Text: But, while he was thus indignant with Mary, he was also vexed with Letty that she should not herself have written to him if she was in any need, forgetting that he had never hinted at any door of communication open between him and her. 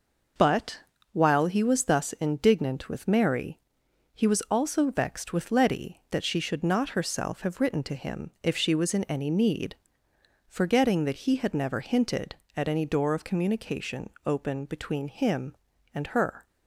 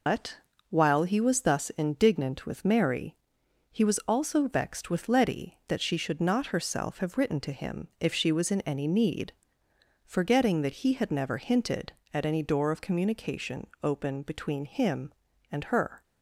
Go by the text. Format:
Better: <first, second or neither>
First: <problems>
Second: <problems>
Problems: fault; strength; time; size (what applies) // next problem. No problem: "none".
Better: first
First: pauses between "communication" and "open"; slight; at 14.0 s; 0.16 s long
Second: loses the start of "But"; at 0.0 s; 110 ms // pauses between "communication" and "open"; slight; at 13.6 s; 0.16 s long